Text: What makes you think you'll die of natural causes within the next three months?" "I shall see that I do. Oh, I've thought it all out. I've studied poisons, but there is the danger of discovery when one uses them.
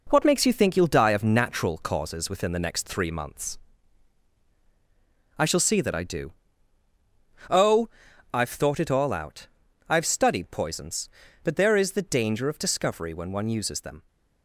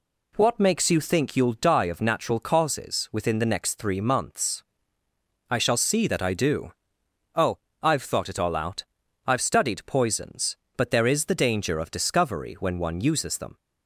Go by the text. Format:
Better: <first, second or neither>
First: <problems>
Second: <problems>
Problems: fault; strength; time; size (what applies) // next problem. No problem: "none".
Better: second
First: gets quieter; noticeable; throughout; 6 dB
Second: none